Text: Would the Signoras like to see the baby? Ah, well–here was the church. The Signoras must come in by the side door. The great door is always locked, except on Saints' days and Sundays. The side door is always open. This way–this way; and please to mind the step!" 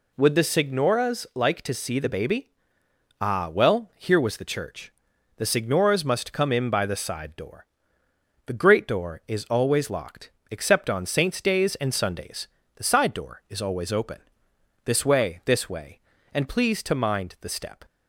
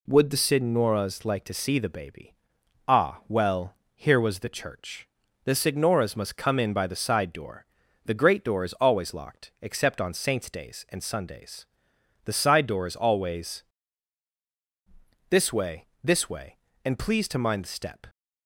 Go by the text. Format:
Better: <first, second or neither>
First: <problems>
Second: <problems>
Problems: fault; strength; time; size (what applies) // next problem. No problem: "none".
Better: first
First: none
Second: skips "open"; at 14.4 s